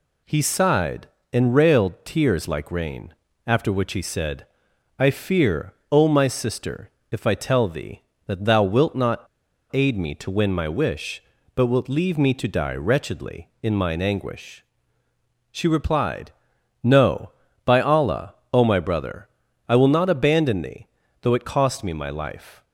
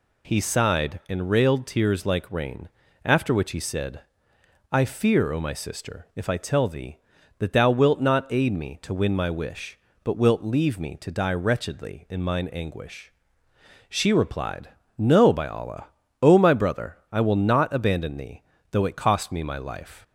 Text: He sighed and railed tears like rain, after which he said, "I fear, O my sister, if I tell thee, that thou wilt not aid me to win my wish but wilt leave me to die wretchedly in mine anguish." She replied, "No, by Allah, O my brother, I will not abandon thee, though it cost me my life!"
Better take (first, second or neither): second